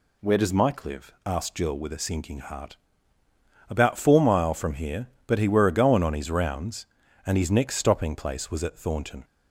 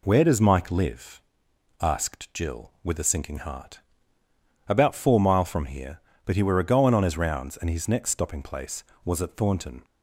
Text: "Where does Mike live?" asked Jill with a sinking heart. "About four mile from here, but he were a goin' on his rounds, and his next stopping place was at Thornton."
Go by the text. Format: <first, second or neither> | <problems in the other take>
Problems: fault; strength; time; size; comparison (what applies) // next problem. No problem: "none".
neither | none